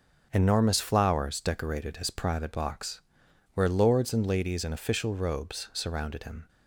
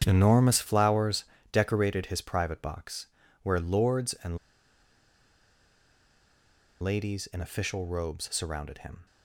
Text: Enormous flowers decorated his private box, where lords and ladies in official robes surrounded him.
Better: first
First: starts louder than the rest; until 1.3 s; 6 dB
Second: starts louder than the rest; strong; until 1.0 s; 8.5 dB // pauses between "flowers" and "decorated"; slight; at 1.2 s; 0.30 s long // pauses between "and" and "ladies"; strong; at 4.3 s; 2.4 s long

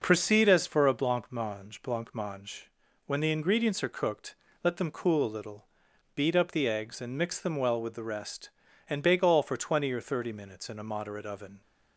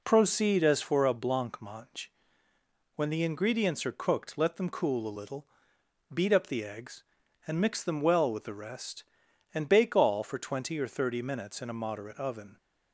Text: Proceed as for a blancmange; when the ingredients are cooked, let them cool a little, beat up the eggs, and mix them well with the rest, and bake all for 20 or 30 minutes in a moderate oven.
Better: second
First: says "blancmange" twice; at 1.8 s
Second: none

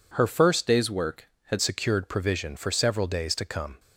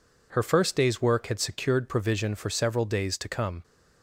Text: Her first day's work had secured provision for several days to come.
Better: second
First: changes voice from "day's" to "had"; from 0.6 to 1.5 s; 0.9 s long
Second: none

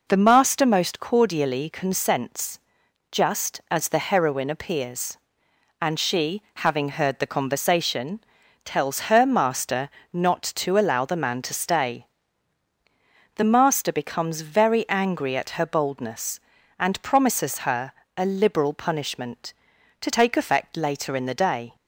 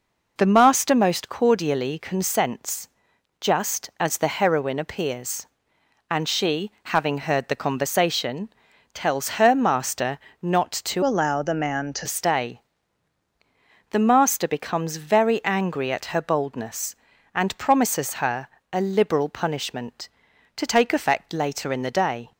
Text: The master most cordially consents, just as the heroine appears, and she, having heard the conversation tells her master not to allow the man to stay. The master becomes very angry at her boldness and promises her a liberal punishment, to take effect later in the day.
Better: first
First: pauses between "conversation" and "tells"; at 8.2 s; 0.42 s long // pauses between "master" and "not"; slight; at 9.8 s; 0.24 s long // pauses between "her" and "a"; slight; at 17.9 s; 0.24 s long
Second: pauses between "conversation" and "tells"; at 8.4 s; 0.42 s long // pauses between "master" and "not"; slight; at 10.1 s; 0.24 s long // changes voice from "allow" to "to"; from 11.0 to 12.0 s; 1.0 s long // pauses between "her" and "a"; slight; at 18.4 s; 0.24 s long

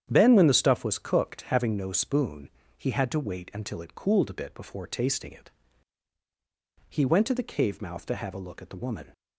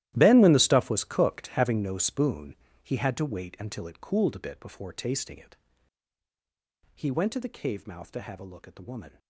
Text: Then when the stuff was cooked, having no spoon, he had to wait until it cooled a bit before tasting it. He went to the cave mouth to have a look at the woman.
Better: first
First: starts louder than the rest; strong; until 1.1 s; 9.5 dB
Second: gets quieter; strong; throughout; 17 dB // starts louder than the rest; strong; until 1.1 s; 14 dB

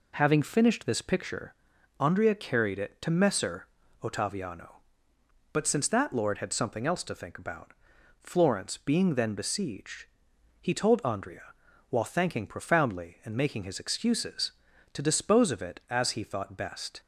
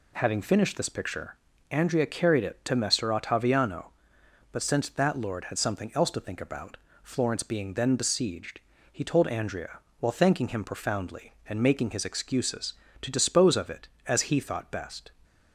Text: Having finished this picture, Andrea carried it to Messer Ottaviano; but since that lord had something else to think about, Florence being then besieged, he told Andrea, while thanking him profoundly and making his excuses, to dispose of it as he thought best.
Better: second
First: pauses between "Messer" and "Ottaviano"; slight; at 3.6 s; 0.34 s long // skips "him"; at 12.4 s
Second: none

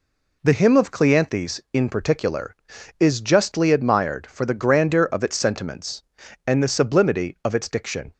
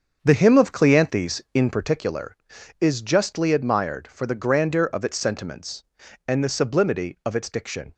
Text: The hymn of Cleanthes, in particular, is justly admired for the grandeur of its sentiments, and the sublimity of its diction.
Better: first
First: none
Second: starts louder than the rest; until 1.9 s; 7 dB

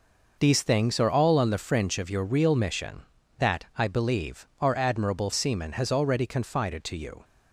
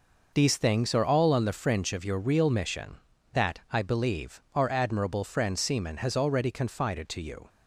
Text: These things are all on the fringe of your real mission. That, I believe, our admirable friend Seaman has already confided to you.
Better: second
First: skips "friend"; at 5.3 s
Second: none

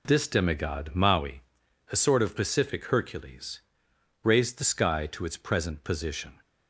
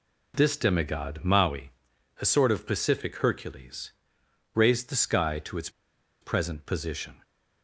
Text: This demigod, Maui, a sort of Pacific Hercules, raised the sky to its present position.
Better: first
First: none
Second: pauses between "its" and "present"; noticeable; at 5.6 s; 0.52 s long

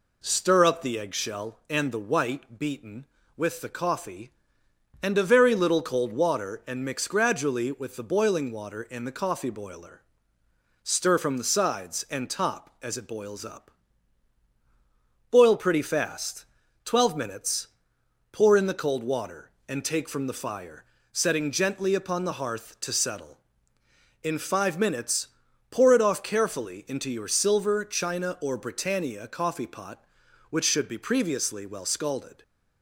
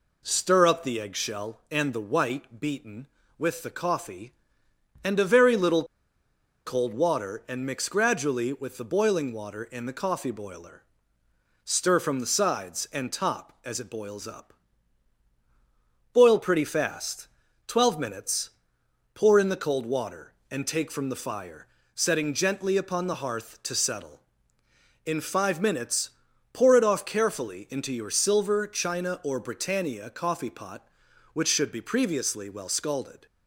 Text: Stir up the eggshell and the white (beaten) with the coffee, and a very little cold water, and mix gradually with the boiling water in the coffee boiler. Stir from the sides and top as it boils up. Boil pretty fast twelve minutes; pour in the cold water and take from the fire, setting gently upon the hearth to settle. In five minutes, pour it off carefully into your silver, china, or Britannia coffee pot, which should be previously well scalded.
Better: first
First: pauses between "fast" and "twelve"; at 16.4 s; 0.40 s long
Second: pauses between "little" and "cold"; noticeable; at 5.8 s; 0.82 s long // pauses between "fast" and "twelve"; at 17.2 s; 0.40 s long

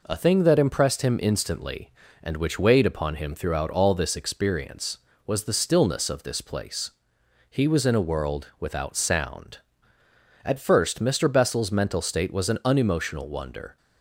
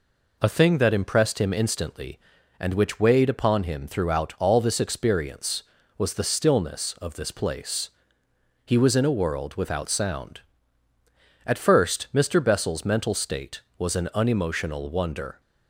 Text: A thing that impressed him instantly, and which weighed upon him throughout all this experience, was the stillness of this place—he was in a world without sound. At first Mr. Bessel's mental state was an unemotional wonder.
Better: neither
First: none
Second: none

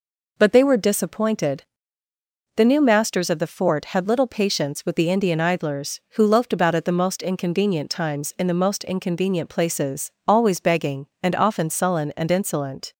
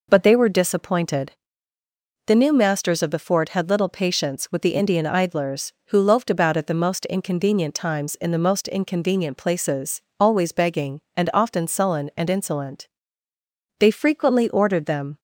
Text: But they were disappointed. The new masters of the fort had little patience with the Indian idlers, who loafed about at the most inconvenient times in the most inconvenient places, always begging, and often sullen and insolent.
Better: first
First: none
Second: goes on to say "They frequently ordered them"; from 13.7 s on; 1.4 s long

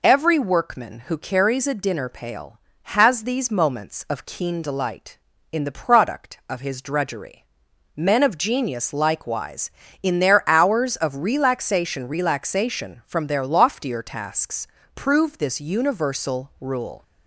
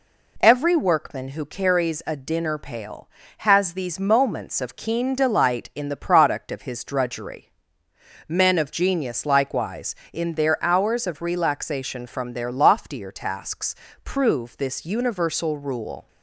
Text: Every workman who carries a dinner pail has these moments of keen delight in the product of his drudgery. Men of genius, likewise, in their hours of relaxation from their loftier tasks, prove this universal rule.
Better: second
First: says "relaxation" twice; at 12.0 s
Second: none

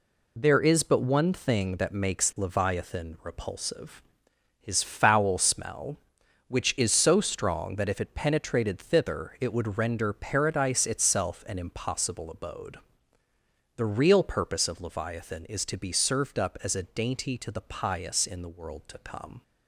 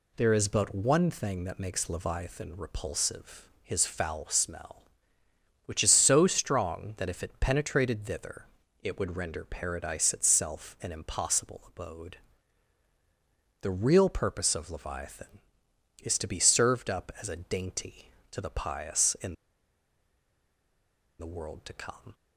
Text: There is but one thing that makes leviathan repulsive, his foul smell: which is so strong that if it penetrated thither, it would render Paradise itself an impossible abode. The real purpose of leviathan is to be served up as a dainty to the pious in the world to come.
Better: first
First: none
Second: pauses between "in" and "the"; strong; at 19.3 s; 1.8 s long

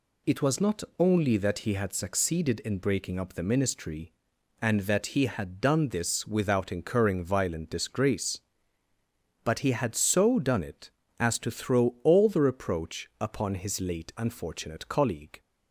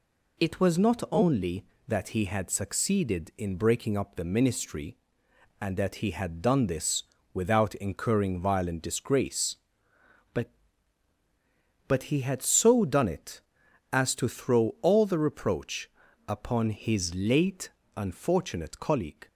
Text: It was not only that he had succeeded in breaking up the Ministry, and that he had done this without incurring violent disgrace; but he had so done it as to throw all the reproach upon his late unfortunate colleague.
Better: first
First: none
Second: pauses between "this" and "without"; slight; at 7.0 s; 0.30 s long // says "but" twice; at 11.8 s // pauses between "reproach" and "upon"; at 15.8 s; 0.38 s long // pauses between "late" and "unfortunate"; slight; at 17.6 s; 0.26 s long

